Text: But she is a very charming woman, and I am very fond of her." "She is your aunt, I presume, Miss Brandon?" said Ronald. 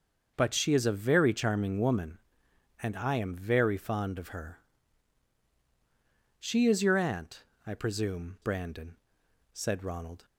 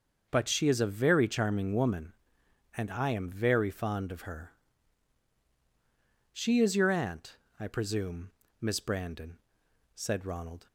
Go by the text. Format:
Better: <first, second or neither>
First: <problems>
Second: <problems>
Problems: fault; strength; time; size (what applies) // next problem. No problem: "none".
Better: second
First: starts louder than the rest; until 1.3 s; 6.5 dB // skips "Miss"; at 8.4 s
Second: starts louder than the rest; until 1.3 s; 6.5 dB